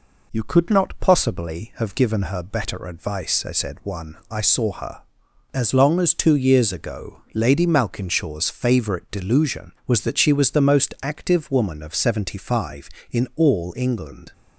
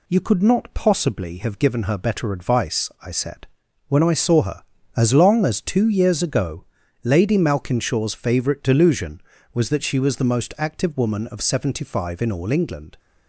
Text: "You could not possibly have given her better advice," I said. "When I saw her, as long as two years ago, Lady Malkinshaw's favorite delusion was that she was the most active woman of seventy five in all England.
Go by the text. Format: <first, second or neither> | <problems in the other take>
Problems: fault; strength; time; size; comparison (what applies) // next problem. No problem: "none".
second | says "One" for "When"; at 3.8 s